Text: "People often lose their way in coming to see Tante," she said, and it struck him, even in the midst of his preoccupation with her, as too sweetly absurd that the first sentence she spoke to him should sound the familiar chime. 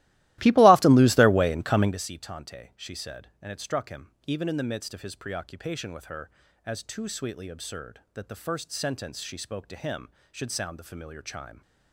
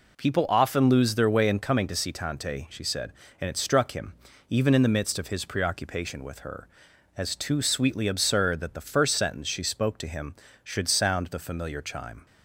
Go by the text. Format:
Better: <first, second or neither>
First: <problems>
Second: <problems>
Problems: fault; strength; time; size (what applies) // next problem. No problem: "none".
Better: second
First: starts louder than the rest; strong; until 2.0 s; 17 dB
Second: none